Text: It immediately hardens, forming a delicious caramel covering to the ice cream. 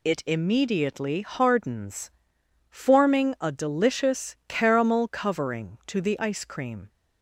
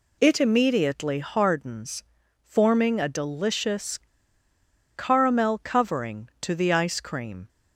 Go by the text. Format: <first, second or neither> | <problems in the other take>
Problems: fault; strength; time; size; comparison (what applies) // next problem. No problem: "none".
first | pauses between "delicious" and "caramel"; noticeable; at 3.9 s; 0.97 s long